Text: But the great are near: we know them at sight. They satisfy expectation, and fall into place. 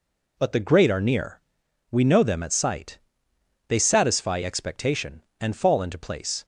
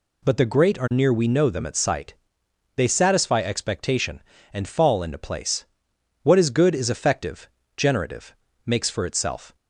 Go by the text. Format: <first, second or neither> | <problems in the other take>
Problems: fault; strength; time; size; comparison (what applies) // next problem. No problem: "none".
first | goes on to say "What is good is effective generative makes for itself"; strong; from 6.2 s on; 3.3 s long